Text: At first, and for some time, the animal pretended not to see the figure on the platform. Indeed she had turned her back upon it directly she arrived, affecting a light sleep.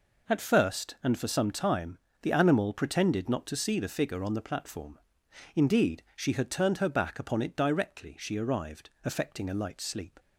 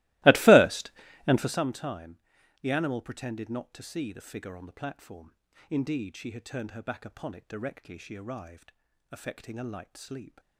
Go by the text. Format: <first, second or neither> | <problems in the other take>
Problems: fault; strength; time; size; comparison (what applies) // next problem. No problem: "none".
first | starts louder than the rest; strong; until 1.7 s; 20 dB